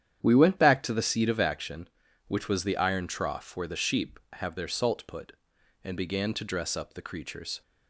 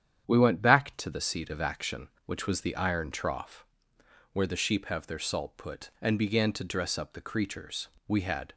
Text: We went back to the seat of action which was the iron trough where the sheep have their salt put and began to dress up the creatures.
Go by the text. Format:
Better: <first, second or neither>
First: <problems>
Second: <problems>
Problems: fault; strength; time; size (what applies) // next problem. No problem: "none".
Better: first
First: starts louder than the rest; strong; until 1.2 s; 9.5 dB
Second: starts louder than the rest; strong; until 1.2 s; 9 dB // pauses between "trough" and "where"; noticeable; at 3.6 s; 0.68 s long // goes on to say "We had"; slight; from 8.0 s on; 0.46 s long